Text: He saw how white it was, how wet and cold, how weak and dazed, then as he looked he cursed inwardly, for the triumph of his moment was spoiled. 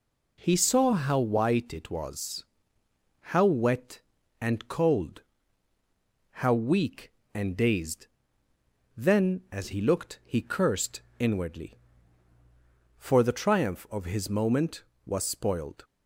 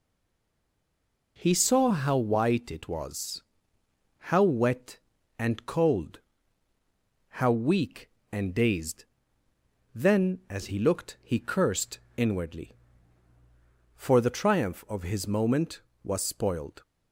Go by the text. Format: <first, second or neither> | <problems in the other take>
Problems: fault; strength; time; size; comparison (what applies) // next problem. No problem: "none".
first | stays silent before the first word; noticeable; until 1.3 s; 1.3 s long // pauses between "cursed" and "inwardly"; slight; at 11.9 s; 0.18 s long; slight in the first